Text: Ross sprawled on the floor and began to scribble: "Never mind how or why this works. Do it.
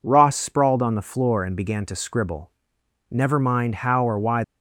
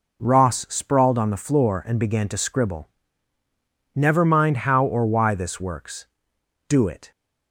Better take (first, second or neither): second